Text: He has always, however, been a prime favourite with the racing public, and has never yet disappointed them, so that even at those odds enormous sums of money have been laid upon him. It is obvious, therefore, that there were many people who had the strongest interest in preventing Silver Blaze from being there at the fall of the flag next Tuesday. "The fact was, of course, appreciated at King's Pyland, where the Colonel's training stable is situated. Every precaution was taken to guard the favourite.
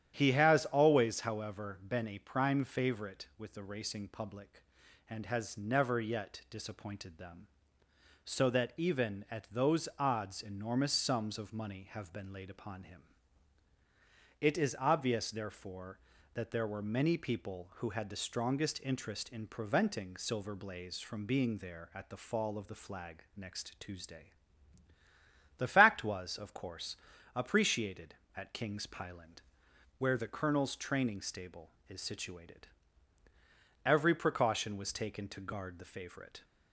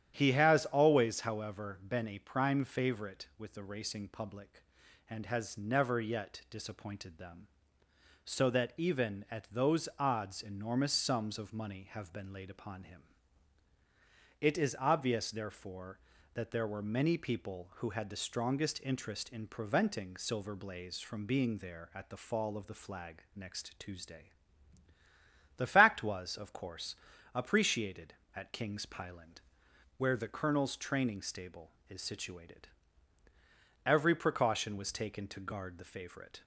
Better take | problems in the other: neither | starts louder than the rest; strong; the same in both

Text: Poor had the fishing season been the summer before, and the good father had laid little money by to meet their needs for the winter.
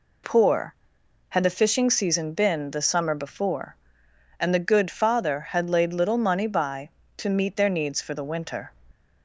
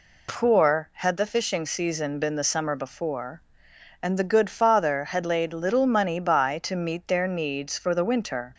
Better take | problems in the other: neither | none

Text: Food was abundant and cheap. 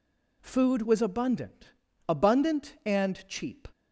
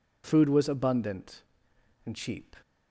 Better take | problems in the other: second | says "abundant" twice; at 2.0 s

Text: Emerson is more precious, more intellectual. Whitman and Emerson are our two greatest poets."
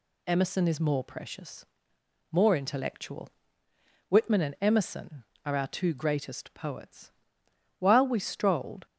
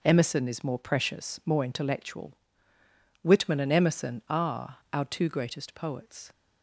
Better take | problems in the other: second | goes on to say "While we strolled"; noticeable; from 7.7 s on; 1.0 s long

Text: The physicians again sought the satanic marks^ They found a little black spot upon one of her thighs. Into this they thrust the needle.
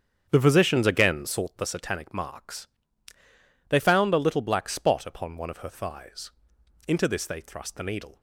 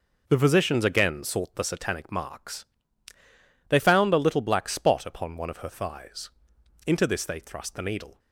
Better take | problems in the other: second | starts louder than the rest; strong; until 1.4 s; 8.5 dB // pauses between "marks" and "They"; at 2.6 s; 1.0 s long; also in the second

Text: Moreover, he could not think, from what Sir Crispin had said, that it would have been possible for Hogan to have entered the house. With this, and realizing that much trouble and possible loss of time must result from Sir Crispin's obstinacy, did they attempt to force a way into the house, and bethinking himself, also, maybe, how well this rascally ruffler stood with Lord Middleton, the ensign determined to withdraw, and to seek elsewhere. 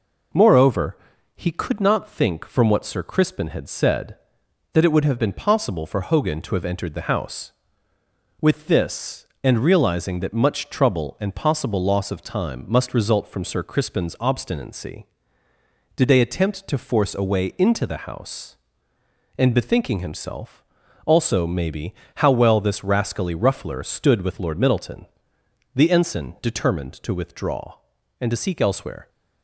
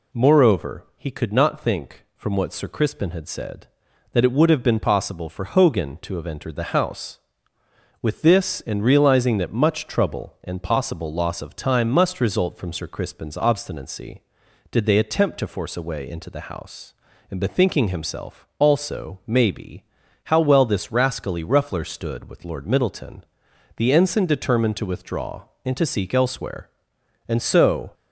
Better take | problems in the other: first | goes on to say "And so"; noticeable; from 27.2 s on; 0.64 s long

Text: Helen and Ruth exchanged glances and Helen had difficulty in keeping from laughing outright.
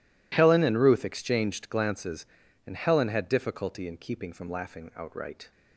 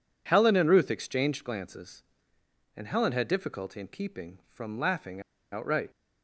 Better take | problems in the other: first | pauses between "laughing" and "outright"; slight; at 5.2 s; 0.31 s long

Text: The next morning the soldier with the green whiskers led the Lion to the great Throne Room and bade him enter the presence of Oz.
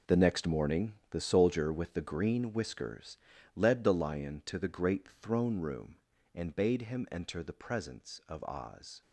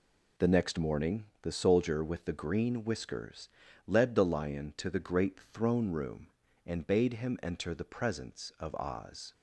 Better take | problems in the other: second | gets quieter; strong; throughout; 11.5 dB // pauses between "morning" and "the"; slight; at 0.9 s; 0.16 s long; slight in the second // pauses between "whiskers" and "led"; at 3.1 s; 0.38 s long; also in the second

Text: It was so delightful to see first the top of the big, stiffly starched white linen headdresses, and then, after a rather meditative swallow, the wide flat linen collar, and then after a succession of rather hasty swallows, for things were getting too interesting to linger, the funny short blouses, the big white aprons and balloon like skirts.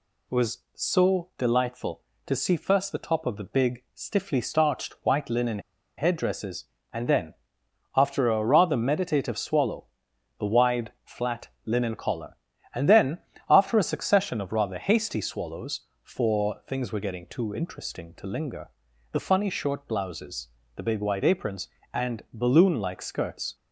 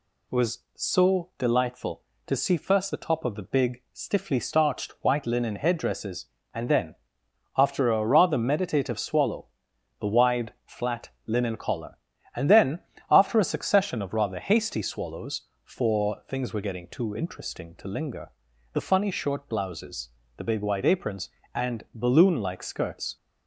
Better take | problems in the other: second | pauses between "linen" and "headdresses"; at 5.5 s; 0.38 s long // pauses between "flat" and "linen"; slight; at 11.4 s; 0.16 s long; slight in the second // pauses between "then" and "after"; slight; at 13.1 s; 0.30 s long; slight in the second

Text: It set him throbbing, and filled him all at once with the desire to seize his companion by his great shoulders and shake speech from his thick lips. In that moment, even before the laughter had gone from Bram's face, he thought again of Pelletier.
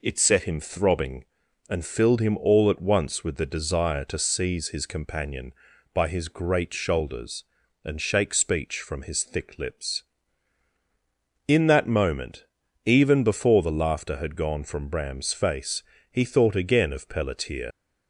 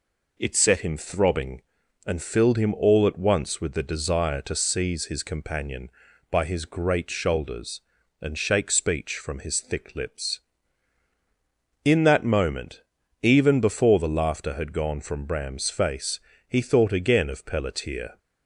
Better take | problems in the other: second | leaves "Pelletier" unfinished; at 17.7 s; 105 ms

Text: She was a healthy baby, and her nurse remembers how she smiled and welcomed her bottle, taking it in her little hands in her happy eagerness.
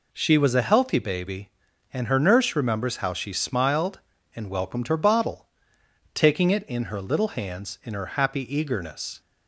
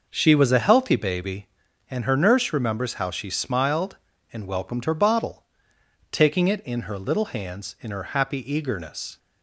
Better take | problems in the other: first | starts louder than the rest; noticeable; until 1.7 s; 5.5 dB

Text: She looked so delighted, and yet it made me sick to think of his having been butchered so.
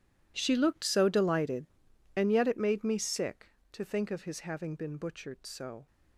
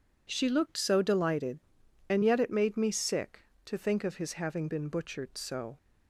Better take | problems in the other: second | gets quieter; strong; throughout; 18.5 dB

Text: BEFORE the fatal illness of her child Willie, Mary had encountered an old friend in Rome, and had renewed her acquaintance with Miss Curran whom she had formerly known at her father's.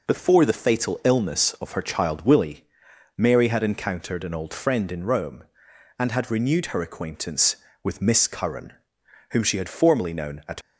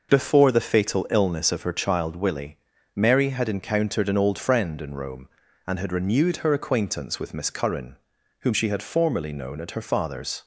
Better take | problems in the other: second | pauses between "Curran" and "whom"; noticeable; at 8.7 s; 0.58 s long; noticeable in the second // stops before "her father's"; at 10.6 s

